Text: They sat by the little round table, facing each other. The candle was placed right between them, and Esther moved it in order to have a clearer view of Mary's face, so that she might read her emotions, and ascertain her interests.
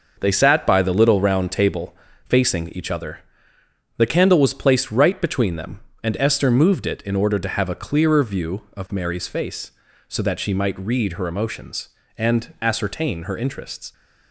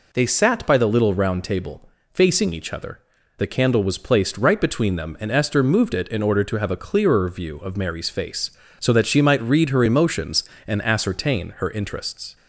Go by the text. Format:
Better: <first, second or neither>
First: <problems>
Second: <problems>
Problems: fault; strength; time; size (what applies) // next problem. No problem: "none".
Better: second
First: gets quieter; strong; throughout; 7.5 dB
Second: none